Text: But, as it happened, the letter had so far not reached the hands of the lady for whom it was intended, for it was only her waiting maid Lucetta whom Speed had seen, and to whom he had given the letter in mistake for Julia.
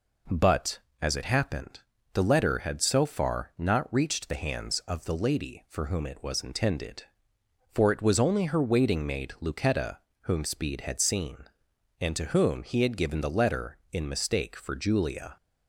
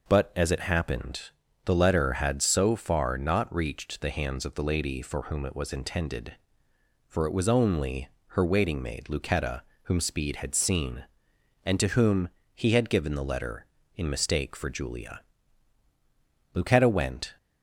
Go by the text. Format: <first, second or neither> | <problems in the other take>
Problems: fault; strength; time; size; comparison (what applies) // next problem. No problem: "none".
first | pauses between "only" and "her"; slight; at 8.0 s; 0.20 s long // pauses between "Lucetta" and "whom"; slight; at 9.6 s; 0.20 s long; slight in the first // pauses between "whom" and "he"; slight; at 12.2 s; 0.26 s long // goes on to say "Lucetta went"; noticeable; from 16.5 s on; 0.82 s long